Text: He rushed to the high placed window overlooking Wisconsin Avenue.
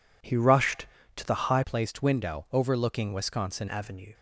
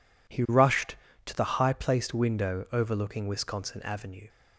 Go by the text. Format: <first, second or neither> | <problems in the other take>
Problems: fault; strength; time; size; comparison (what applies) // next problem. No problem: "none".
second | changes voice from "placed" to "Wisconsin"; from 1.6 to 3.6 s; 2.0 s long